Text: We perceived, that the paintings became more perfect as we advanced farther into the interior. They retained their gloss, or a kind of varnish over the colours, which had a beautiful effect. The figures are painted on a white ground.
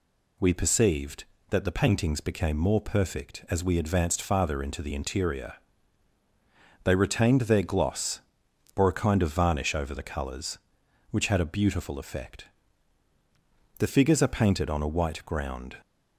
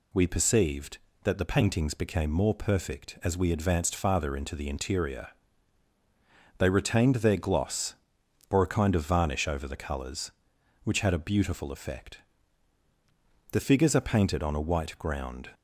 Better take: neither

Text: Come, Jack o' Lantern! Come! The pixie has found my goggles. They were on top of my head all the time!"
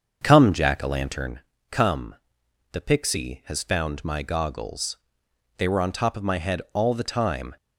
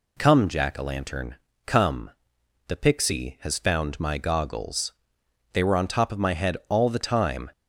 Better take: second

